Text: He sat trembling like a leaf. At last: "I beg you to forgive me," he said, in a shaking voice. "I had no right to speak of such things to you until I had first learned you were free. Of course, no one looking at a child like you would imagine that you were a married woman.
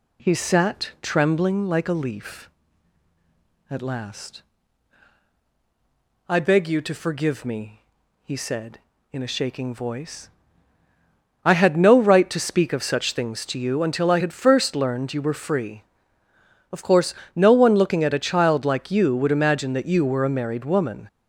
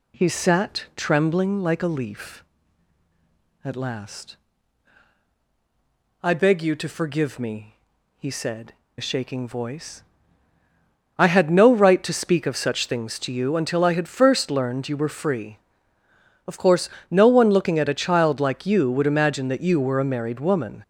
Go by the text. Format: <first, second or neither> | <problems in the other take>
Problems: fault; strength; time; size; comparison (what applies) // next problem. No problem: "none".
first | skips "in"; at 8.8 s